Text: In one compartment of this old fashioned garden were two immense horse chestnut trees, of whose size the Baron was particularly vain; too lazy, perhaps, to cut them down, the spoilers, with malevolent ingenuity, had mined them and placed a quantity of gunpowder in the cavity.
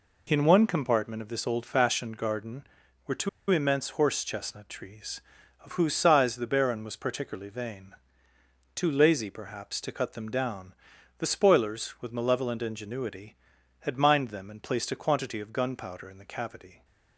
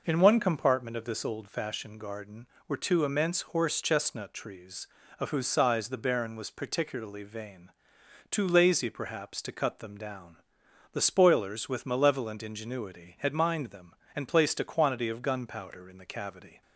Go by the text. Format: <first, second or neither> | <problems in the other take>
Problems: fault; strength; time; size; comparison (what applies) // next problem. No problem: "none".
second | pauses between "two" and "immense"; slight; at 3.2 s; 0.21 s long